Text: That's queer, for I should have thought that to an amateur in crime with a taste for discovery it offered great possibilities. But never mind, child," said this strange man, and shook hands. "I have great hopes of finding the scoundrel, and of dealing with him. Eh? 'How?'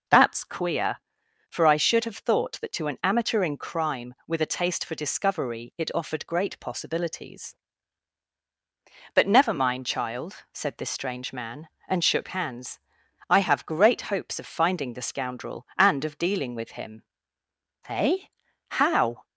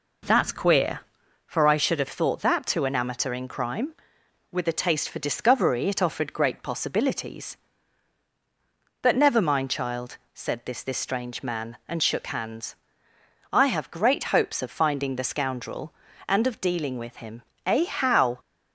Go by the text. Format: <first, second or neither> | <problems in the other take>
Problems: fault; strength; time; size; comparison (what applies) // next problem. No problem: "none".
first | says "this" twice; at 10.8 s